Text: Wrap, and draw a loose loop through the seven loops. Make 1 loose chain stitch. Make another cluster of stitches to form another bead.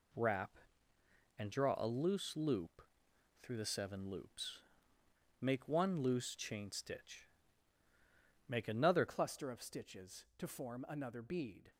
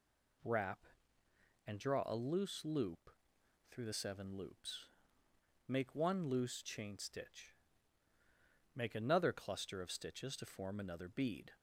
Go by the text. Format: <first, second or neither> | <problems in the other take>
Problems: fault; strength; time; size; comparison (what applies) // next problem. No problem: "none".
second | pauses between "loop" and "through"; noticeable; at 2.8 s; 0.60 s long; noticeable in the second // changes voice at "cluster"; from 9.0 s on; 2.7 s long